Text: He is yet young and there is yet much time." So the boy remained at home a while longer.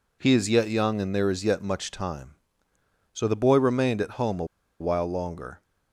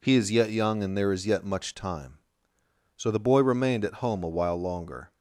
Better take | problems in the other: second | pauses between "a" and "while"; slight; at 4.4 s; 0.35 s long

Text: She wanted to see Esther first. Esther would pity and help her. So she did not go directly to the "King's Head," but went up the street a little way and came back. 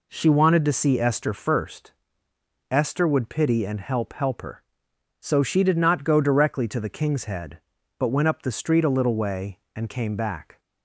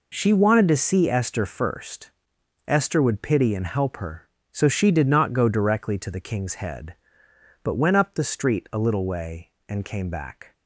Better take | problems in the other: second | says "help" twice; at 4.1 s

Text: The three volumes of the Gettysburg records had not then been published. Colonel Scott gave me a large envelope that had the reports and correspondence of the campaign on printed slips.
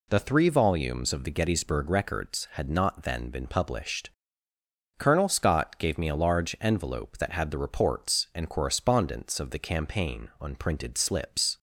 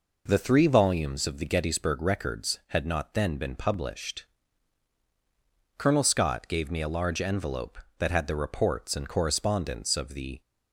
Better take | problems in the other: first | stops before "campaign on printed slips"; at 10.4 s

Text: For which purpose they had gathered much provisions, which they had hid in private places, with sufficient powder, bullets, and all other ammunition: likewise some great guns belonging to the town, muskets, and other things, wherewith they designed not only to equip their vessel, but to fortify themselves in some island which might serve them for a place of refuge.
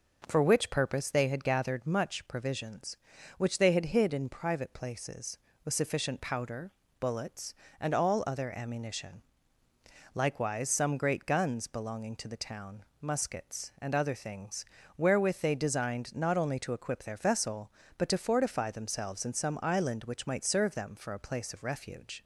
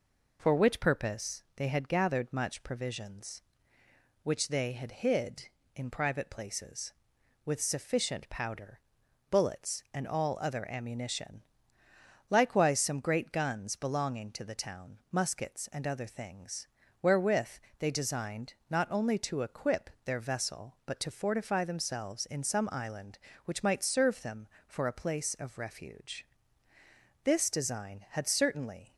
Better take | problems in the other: first | pauses between "wherewith" and "they"; slight; at 17.5 s; 0.18 s long // pauses between "designed" and "not"; slight; at 18.5 s; 0.16 s long // goes on to say "This design had certainly"; strong; from 27.2 s on; 1.7 s long

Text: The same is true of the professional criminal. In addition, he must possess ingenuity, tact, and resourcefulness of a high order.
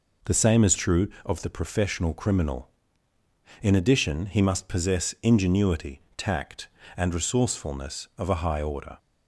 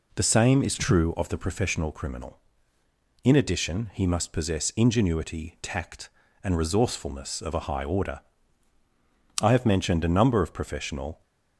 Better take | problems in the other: first | goes on to say "I have mentioned a number of professional"; strong; from 9.4 s on; 1.8 s long

